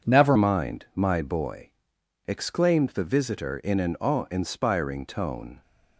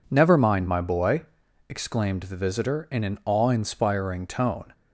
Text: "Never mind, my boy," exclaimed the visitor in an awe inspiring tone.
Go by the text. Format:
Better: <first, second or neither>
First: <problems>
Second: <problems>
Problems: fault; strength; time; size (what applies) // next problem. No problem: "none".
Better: second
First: changes voice at "mind"; from 0.3 s on; 5.3 s long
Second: none